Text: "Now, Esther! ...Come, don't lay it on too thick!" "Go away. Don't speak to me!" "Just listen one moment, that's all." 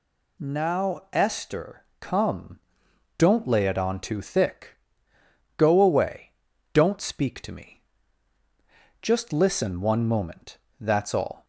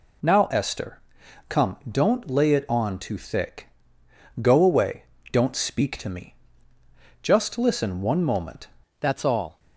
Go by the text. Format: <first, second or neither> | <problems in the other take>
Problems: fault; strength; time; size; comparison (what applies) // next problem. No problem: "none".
first | changes voice at "that's"; from 9.0 s on; 0.5 s long